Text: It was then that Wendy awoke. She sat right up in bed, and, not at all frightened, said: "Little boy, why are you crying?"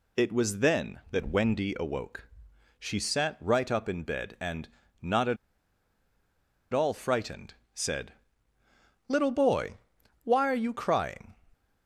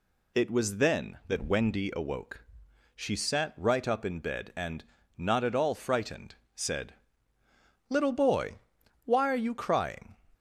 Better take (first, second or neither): second